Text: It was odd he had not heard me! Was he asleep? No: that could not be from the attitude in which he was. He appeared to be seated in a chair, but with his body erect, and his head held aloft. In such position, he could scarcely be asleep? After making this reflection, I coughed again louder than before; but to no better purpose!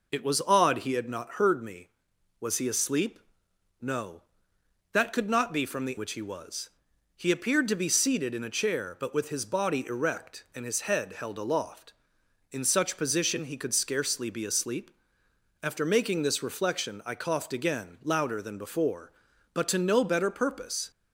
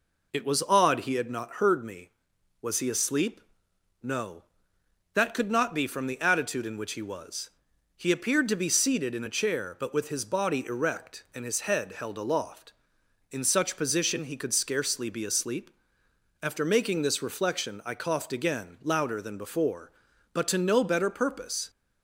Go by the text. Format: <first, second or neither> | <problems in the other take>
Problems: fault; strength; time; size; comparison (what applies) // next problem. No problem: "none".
second | skips "attitude in"; at 5.9 s